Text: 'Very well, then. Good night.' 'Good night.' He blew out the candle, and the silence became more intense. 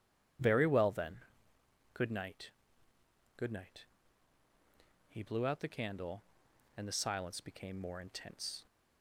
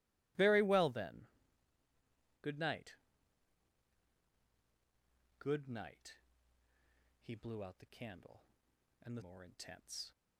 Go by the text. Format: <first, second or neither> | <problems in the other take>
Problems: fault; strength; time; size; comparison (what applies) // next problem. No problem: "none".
first | skips "silence became"; at 9.2 s